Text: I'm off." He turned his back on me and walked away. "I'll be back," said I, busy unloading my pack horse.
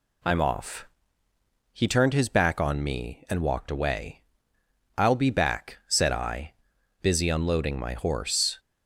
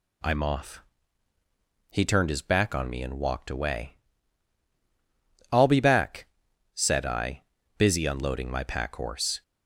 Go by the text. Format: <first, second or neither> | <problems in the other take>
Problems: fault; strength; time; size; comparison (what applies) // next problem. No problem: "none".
second | skips "pack"; at 7.9 s